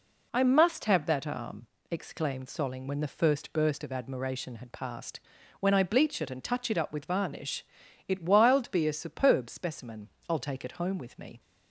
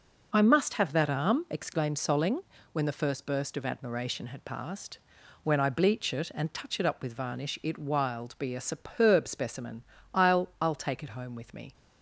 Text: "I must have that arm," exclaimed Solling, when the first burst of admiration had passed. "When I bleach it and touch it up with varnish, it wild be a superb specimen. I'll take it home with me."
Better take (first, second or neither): first